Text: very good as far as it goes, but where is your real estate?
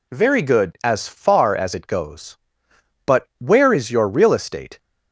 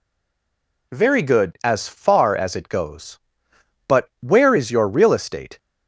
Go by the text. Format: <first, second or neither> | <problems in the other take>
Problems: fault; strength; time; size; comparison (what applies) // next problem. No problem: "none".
first | stays silent before the first word; slight; until 0.9 s; 0.9 s long